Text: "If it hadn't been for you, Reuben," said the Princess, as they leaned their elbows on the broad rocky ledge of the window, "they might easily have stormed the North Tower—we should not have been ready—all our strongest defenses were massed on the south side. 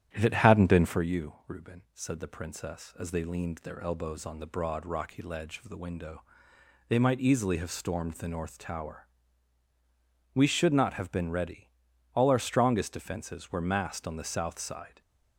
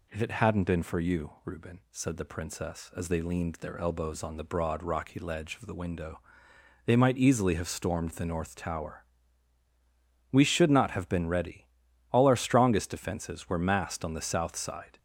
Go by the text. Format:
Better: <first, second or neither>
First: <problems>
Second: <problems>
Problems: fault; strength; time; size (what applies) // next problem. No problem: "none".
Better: second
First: starts louder than the rest; strong; until 1.1 s; 10.5 dB // stays silent after the last word; slight; from 14.8 s on; 0.5 s long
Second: none